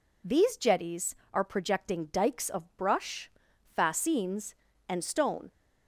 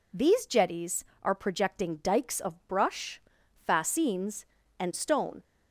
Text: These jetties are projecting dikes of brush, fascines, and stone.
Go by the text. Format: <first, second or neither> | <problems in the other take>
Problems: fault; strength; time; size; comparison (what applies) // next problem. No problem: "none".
neither | none